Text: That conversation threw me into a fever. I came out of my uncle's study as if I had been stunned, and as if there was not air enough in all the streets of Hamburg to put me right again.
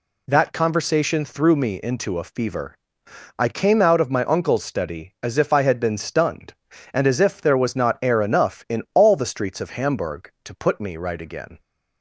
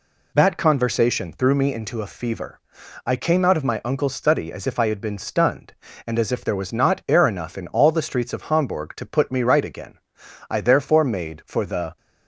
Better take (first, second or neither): first